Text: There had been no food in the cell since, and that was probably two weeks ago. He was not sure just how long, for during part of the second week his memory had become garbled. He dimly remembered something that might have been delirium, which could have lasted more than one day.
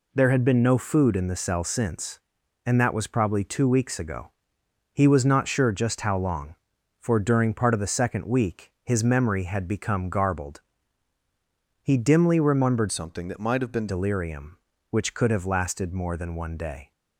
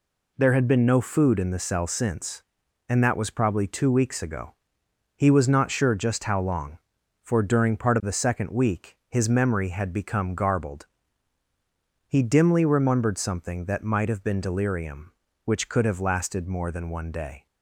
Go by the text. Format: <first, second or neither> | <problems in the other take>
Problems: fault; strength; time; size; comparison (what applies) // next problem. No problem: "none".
second | changes voice from "something" to "been"; from 12.9 to 13.8 s; 0.9 s long